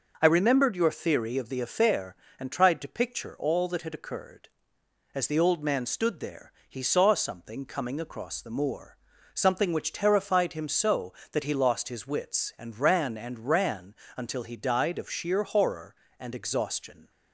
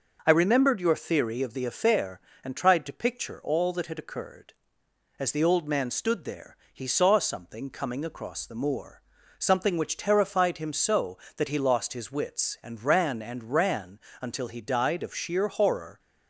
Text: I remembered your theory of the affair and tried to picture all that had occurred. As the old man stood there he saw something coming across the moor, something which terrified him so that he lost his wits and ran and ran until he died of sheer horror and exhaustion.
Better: first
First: pauses between "there" and "he"; slight; at 6.5 s; 0.18 s long // pauses between "ran" and "until"; slight; at 13.9 s; 0.22 s long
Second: pauses between "there" and "he"; slight; at 6.5 s; 0.18 s long // pauses between "ran" and "until"; slight; at 13.9 s; 0.22 s long // stops before "and exhaustion"; at 15.9 s

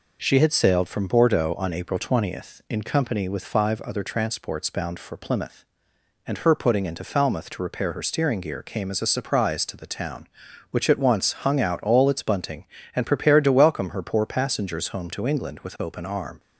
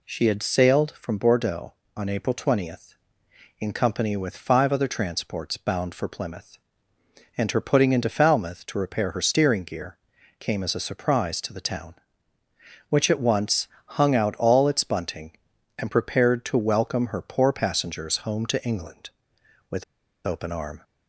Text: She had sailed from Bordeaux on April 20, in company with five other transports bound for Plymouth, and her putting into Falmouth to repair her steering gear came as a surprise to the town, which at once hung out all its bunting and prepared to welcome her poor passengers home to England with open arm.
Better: first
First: none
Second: pauses between "gear" and "came"; at 9.9 s; 0.42 s long // pauses between "once" and "hung"; slight; at 13.6 s; 0.18 s long // pauses between "with" and "open"; at 19.8 s; 0.43 s long

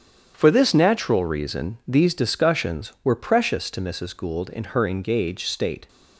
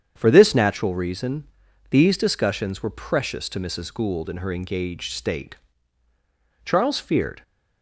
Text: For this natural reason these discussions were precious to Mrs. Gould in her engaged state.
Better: first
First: starts louder than the rest; strong; until 1.3 s; 8.5 dB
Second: starts louder than the rest; strong; until 1.1 s; 8 dB // pauses between "reason" and "these"; noticeable; at 1.4 s; 0.46 s long // goes on to say "Charles feared"; noticeable; from 6.6 s on; 0.78 s long

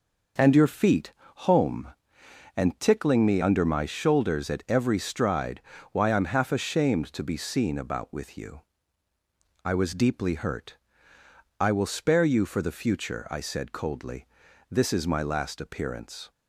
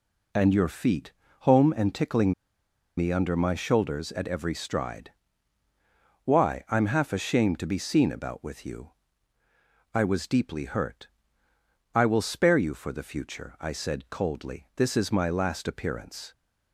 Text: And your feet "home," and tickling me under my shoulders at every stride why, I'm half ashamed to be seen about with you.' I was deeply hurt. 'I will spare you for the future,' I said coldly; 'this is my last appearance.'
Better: first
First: pauses between "feet" and "home"; slight; at 1.1 s; 0.34 s long // pauses between "stride" and "why"; slight; at 5.6 s; 0.32 s long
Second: pauses between "feet" and "home"; slight; at 1.1 s; 0.28 s long // pauses between "tickling" and "me"; noticeable; at 2.3 s; 0.65 s long // pauses between "stride" and "why"; at 5.1 s; 1.1 s long

